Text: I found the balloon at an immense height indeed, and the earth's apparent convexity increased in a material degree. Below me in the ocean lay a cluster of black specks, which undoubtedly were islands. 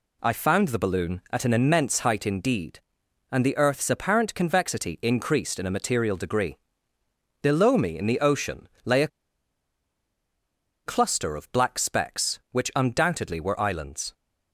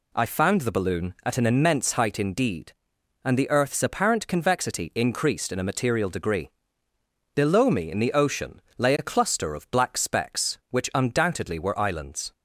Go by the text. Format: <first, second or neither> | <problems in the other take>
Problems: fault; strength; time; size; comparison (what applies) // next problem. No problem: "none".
second | pauses between "ocean" and "lay"; slight; at 8.6 s; 0.16 s long; slight in the second // pauses between "a" and "cluster"; strong; at 9.1 s; 1.7 s long